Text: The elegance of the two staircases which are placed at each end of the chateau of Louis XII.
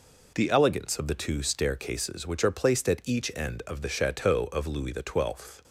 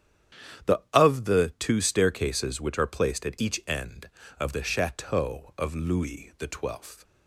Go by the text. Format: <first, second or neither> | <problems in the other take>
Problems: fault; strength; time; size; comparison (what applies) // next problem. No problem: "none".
first | starts louder than the rest; strong; until 1.8 s; 9.5 dB // skips "elegance"; at 0.8 s